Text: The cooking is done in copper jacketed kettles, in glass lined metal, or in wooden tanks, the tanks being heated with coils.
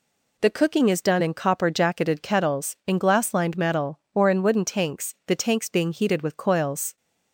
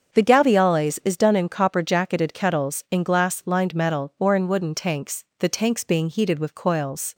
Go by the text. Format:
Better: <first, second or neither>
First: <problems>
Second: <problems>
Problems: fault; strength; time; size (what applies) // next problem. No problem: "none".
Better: first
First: none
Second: starts louder than the rest; until 1.1 s; 7 dB // says "gaviales" for "cooking"; at 0.2 s